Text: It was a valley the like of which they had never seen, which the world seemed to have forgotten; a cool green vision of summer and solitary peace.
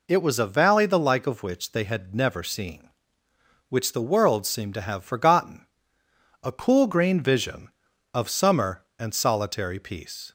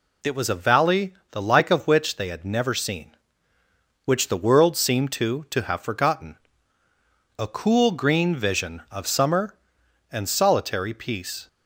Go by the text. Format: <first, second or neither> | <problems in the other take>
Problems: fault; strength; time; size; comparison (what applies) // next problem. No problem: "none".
first | pauses between "valley" and "the"; slight; at 1.1 s; 0.18 s long // says "to" twice; at 5.4 s